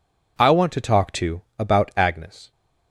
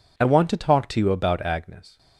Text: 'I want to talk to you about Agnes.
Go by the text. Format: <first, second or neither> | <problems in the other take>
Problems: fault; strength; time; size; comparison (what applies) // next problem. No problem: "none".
second | skips "you"; at 1.4 s